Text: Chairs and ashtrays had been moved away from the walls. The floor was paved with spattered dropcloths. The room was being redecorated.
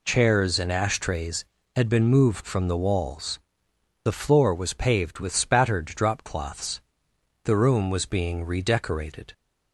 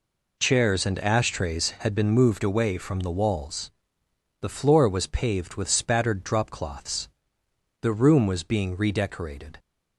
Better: second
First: skips "away"; at 2.4 s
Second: none

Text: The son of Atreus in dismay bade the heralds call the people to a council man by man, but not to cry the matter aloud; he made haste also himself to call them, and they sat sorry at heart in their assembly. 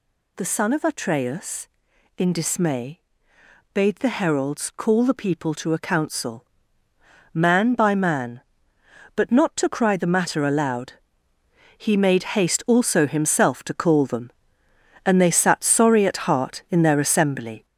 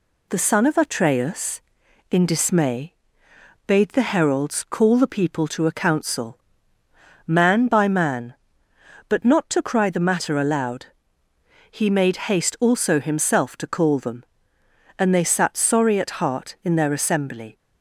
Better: second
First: gets louder; noticeable; throughout; 5.5 dB // pauses between "dismay" and "bade"; noticeable; at 2.9 s; 0.74 s long // pauses between "council" and "man"; noticeable; at 6.4 s; 0.88 s long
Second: pauses between "dismay" and "bade"; noticeable; at 2.9 s; 0.74 s long // pauses between "council" and "man"; noticeable; at 6.3 s; 0.88 s long

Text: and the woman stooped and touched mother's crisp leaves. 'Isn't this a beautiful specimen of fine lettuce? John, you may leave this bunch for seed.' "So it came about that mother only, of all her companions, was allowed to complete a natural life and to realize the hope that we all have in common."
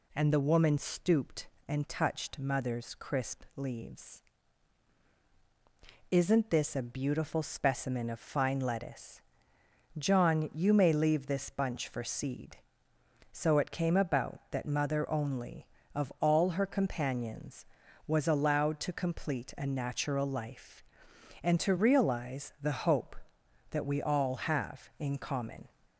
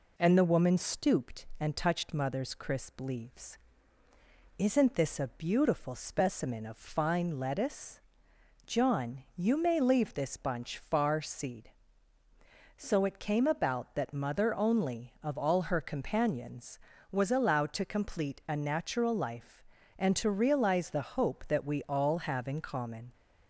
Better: first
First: none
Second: says "far" for "for"; at 10.7 s

